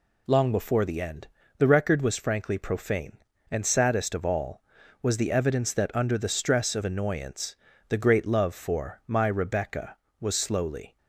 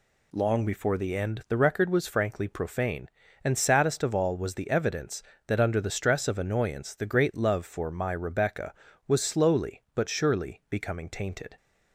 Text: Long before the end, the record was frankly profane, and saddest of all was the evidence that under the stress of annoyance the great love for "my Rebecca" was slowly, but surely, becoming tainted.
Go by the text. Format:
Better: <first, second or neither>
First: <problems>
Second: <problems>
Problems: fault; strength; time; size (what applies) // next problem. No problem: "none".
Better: second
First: pauses between "annoyance" and "the"; slight; at 7.5 s; 0.32 s long // stops before "but surely becoming tainted"; at 10.9 s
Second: none